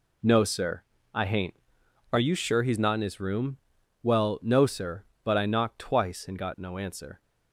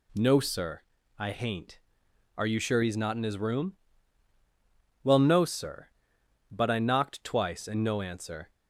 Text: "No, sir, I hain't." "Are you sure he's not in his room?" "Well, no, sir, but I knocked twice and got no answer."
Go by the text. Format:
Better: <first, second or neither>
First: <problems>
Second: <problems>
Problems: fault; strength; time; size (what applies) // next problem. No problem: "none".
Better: first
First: none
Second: skips "got"; at 7.8 s